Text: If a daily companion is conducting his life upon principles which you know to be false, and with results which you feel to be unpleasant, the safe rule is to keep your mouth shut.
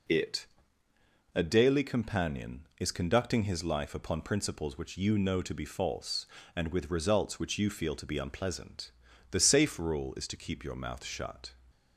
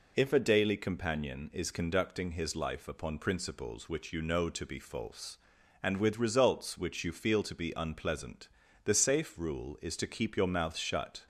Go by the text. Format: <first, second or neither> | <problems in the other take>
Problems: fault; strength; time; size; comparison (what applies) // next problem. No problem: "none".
second | says "It" for "If"; at 0.0 s